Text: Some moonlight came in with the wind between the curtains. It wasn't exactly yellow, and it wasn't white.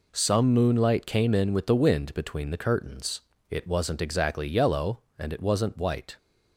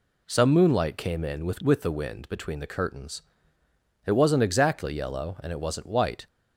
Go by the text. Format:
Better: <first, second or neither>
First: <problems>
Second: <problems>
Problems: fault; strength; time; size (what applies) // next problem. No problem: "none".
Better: first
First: none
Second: says "with" twice; at 1.6 s